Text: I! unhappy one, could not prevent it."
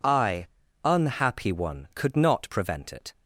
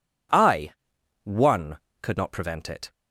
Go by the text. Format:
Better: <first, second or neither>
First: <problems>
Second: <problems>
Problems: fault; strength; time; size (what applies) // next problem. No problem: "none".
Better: first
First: none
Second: skips "unhappy"; at 0.9 s